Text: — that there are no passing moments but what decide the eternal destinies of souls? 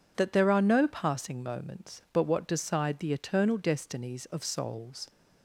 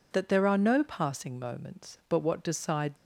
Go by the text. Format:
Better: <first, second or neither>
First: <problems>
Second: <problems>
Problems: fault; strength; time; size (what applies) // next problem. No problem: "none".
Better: first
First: none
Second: stops before "the eternal destinies of souls"; at 2.9 s